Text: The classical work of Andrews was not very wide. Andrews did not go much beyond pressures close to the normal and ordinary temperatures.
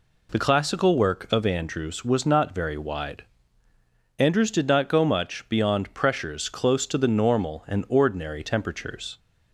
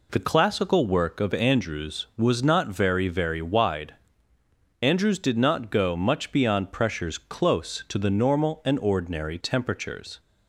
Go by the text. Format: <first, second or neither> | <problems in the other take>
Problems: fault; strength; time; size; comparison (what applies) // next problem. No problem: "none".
first | says "very" twice; at 3.0 s